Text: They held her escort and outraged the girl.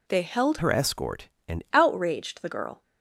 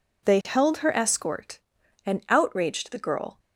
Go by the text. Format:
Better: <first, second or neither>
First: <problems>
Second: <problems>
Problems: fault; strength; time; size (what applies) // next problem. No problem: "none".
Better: second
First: changes voice from "her" to "and"; from 0.5 to 1.6 s; 1.1 s long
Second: none